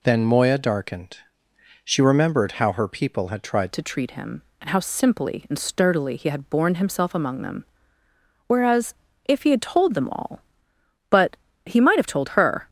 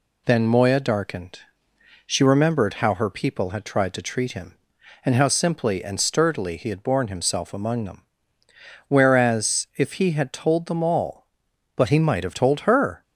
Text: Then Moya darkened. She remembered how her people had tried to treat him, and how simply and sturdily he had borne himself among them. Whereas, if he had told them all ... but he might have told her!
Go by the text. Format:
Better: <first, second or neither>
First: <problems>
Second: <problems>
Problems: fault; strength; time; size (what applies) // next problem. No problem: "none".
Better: second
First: changes voice at "to"; from 3.7 s on; 8.9 s long // pauses between "but" and "he"; slight; at 11.3 s; 0.28 s long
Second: none